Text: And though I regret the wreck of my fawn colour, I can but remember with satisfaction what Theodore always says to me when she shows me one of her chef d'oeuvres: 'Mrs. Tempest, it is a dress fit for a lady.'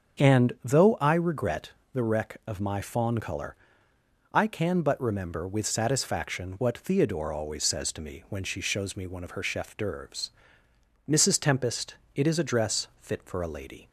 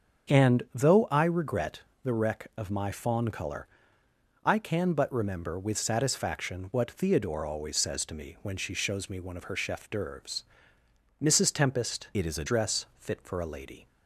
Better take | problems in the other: first | starts louder than the rest; until 1.4 s; 6.5 dB; also in the first // pauses between "regret" and "the"; slight; at 1.8 s; 0.22 s long; slight in the first // changes voice from "it" to "a"; from 12.1 to 12.4 s; 0.3 s long

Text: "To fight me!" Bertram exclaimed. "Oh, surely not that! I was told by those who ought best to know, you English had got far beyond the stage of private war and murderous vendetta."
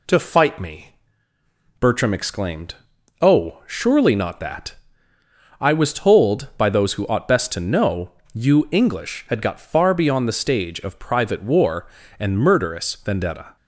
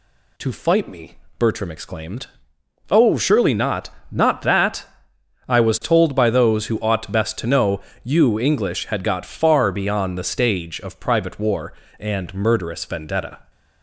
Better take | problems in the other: first | says "not" twice; at 4.1 s

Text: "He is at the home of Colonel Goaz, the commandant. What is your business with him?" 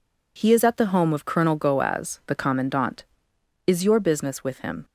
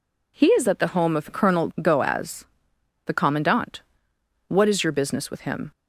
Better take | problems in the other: second | skips "What"; at 3.3 s

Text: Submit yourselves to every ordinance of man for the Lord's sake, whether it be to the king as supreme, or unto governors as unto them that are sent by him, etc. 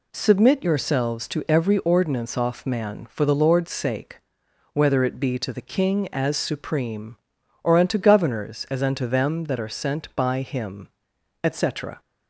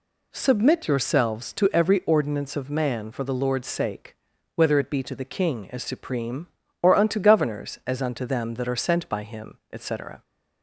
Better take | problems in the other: second | says "off" for "of"; at 2.3 s

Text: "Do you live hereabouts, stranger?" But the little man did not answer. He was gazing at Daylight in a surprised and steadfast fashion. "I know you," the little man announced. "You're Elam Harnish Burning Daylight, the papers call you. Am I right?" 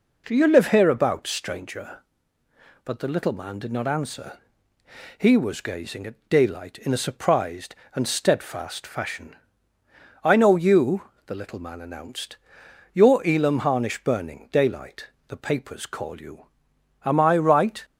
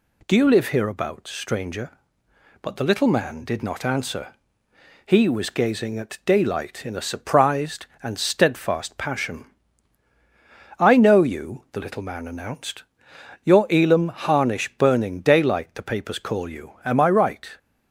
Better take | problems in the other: first | says "passion" for "fashion"; at 8.9 s

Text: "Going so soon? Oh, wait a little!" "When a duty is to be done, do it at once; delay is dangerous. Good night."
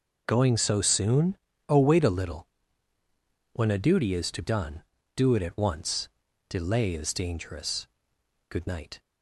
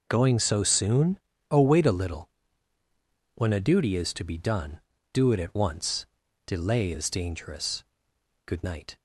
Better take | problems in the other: second | skips "be"; at 4.4 s

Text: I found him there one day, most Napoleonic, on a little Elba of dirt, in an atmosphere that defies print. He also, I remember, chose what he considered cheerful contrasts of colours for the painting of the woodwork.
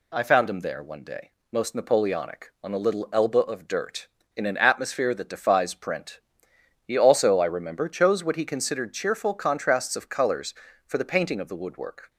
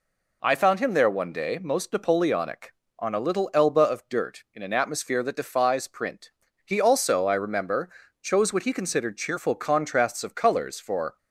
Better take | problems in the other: first | stops before "the painting of the woodwork"; at 11.1 s

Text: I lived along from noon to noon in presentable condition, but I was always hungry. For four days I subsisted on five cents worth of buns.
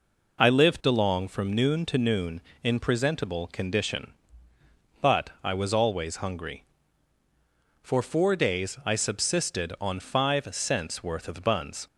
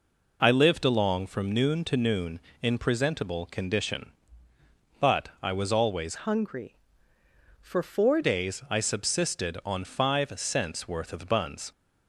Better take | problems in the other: first | changes voice from "hungry" to "four"; from 6.1 to 8.2 s; 2.1 s long

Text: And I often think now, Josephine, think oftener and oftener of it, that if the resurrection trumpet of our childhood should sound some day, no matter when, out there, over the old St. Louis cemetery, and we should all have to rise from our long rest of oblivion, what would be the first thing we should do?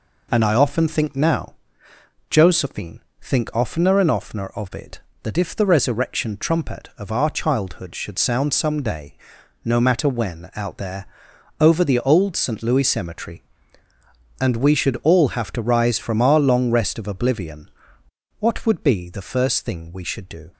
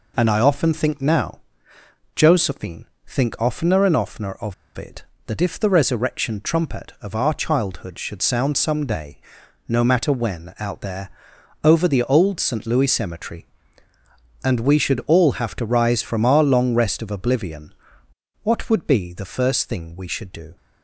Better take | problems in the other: first | pauses between "of" and "it"; slight; at 4.5 s; 0.23 s long

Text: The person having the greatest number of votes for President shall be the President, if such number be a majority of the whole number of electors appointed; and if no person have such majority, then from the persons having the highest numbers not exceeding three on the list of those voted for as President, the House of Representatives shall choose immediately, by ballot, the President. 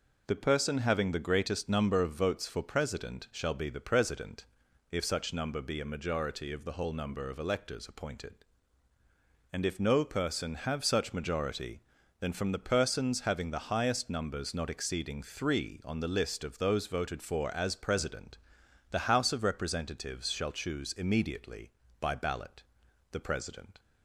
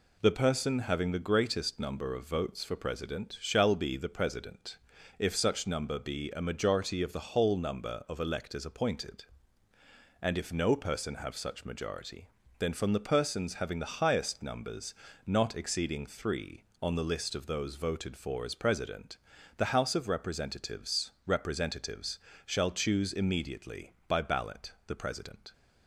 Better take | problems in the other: first | pauses between "numbers" and "not"; slight; at 14.9 s; 0.32 s long // says "Representatives" twice; at 21.2 s

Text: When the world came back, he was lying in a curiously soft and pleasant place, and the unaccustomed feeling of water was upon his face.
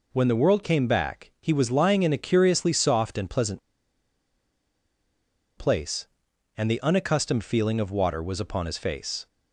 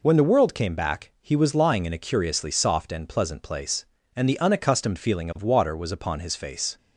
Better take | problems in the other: second | pauses between "pleasant" and "place"; strong; at 3.5 s; 1.9 s long

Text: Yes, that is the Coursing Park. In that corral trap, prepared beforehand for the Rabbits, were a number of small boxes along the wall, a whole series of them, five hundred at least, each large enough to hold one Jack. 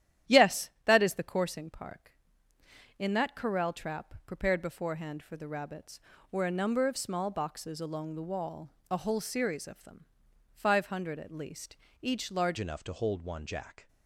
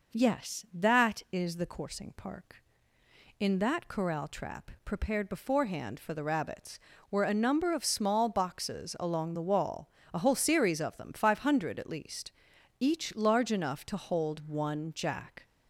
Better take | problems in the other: second | starts louder than the rest; strong; until 1.4 s; 11 dB // changes voice at "enough"; from 12.5 s on; 1.3 s long

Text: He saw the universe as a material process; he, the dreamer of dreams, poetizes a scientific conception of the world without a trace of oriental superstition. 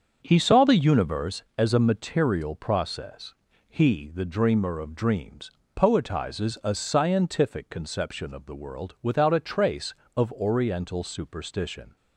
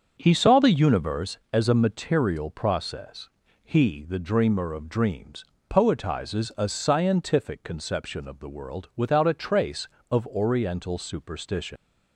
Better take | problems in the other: first | starts louder than the rest; until 1.1 s; 7 dB; also in the first // leaves "superstition" unfinished; at 11.7 s; 140 ms

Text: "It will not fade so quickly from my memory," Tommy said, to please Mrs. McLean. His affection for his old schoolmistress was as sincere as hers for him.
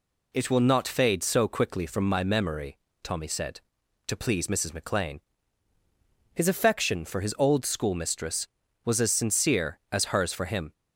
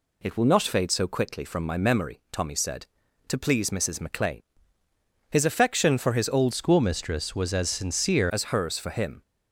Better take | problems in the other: first | changes voice from "schoolmistress" to "sincere"; from 6.5 to 8.3 s; 1.8 s long

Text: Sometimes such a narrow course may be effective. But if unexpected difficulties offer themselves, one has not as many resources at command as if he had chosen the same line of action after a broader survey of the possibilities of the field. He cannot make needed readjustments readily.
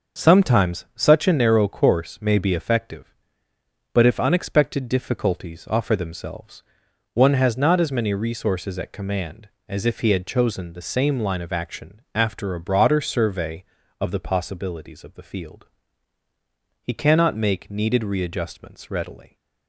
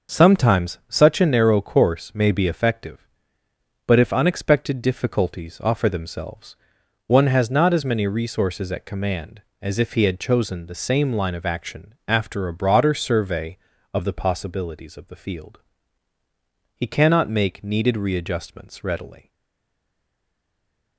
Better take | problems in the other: first | starts louder than the rest; until 1.2 s; 6 dB; also in the first // stays silent after the last word; noticeable; from 19.2 s on; 1.7 s long

